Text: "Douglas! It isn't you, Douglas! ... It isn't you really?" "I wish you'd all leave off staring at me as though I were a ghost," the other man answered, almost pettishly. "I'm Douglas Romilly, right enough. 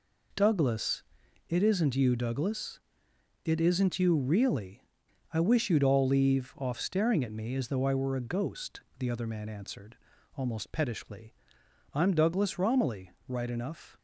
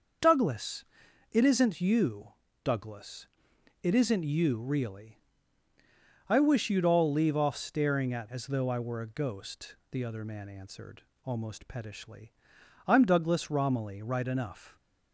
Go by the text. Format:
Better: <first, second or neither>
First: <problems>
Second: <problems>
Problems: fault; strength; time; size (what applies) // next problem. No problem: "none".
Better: first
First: none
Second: starts louder than the rest; until 1.6 s; 6 dB // skips "me"; at 8.3 s